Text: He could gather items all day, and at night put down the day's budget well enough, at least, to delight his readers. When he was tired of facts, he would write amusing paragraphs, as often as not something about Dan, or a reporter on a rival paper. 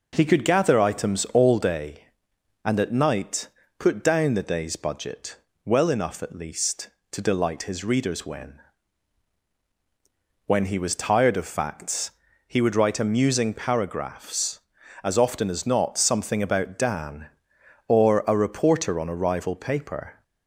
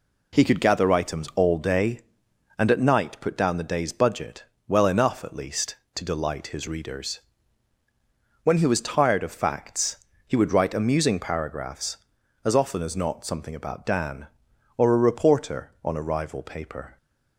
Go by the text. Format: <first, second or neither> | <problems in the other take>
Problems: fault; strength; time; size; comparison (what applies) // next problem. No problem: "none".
second | pauses between "night" and "put"; slight; at 3.4 s; 0.32 s long // pauses between "budget" and "well"; slight; at 5.3 s; 0.28 s long; slight in the second // says "When" twice; at 10.4 s